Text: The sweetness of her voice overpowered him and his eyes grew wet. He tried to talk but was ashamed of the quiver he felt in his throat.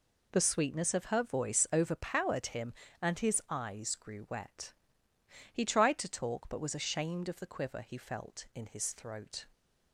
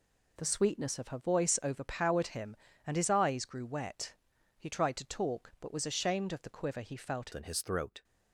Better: first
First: none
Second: changes voice at "in"; from 7.3 s on; 0.7 s long

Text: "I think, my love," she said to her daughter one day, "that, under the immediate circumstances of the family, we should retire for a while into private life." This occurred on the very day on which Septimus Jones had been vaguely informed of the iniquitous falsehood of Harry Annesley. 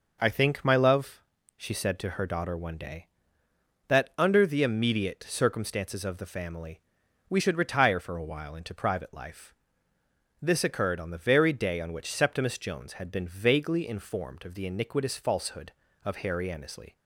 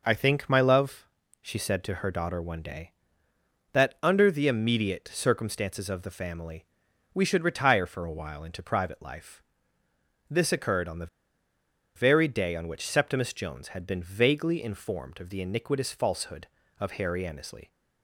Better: first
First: none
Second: pauses between "the" and "very"; noticeable; at 11.0 s; 0.89 s long

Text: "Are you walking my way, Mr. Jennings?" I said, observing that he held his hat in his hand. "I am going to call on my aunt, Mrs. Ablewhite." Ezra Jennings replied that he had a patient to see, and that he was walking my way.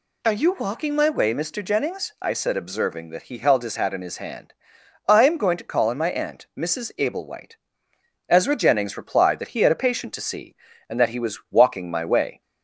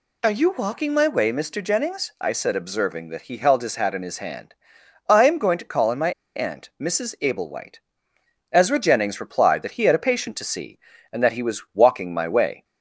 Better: first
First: none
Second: pauses between "my" and "aunt"; slight; at 6.1 s; 0.24 s long

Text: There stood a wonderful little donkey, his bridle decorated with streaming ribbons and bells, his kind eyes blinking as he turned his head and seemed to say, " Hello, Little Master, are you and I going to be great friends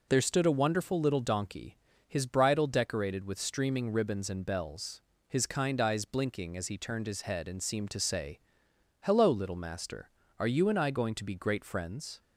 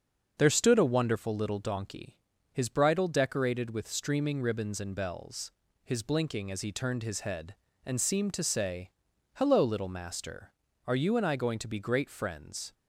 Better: first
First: starts louder than the rest; noticeable; until 1.1 s; 6 dB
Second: starts louder than the rest; until 1.3 s; 7 dB // skips "kind eyes"; at 6.0 s

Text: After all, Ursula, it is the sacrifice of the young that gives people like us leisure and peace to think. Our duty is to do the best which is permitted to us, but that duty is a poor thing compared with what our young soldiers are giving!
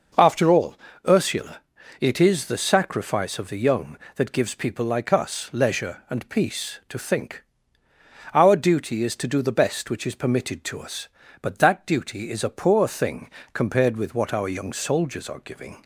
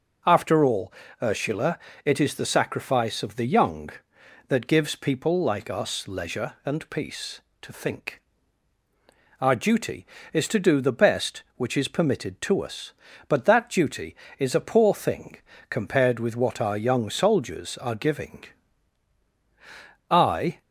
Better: first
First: pauses between "thing" and "compared"; slight; at 13.3 s; 0.22 s long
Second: pauses between "thing" and "compared"; slight; at 15.3 s; 0.34 s long // goes on to say "I"; from 20.1 s on; 0.50 s long

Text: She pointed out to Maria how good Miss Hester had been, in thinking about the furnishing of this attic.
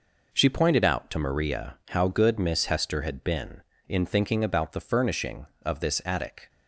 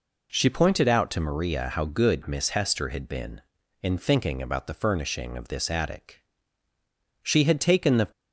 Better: first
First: none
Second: goes on to say "She had taken the"; noticeable; from 7.2 s on; 0.86 s long

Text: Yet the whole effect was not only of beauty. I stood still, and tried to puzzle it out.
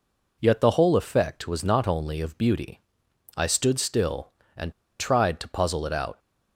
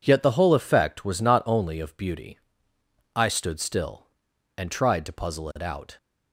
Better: second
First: pauses between "and" and "tried"; slight; at 4.7 s; 0.27 s long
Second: none

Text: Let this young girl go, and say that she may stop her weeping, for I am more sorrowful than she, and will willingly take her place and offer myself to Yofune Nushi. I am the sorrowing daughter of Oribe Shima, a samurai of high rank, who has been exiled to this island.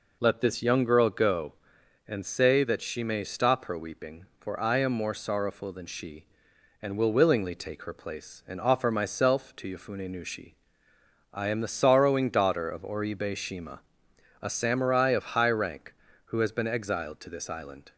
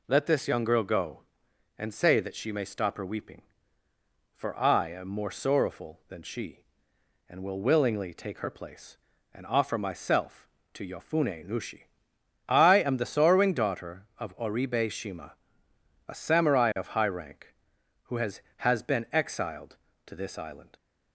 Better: first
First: none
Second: says "has" twice; at 18.5 s

